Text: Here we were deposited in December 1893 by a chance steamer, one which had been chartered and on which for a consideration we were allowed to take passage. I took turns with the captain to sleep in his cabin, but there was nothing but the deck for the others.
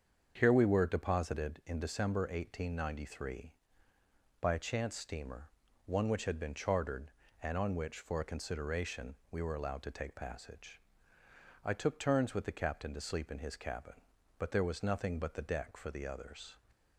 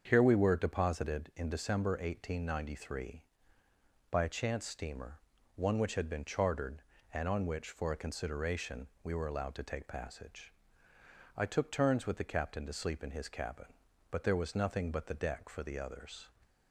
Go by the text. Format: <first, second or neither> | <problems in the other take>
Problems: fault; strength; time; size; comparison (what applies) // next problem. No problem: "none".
neither | starts louder than the rest; strong; the same in both // pauses between "consideration" and "we"; slight; the same in both